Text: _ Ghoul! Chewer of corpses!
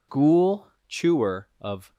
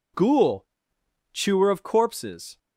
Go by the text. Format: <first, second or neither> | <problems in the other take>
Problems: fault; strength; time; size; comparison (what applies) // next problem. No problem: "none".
second | stops before "corpses"; at 1.9 s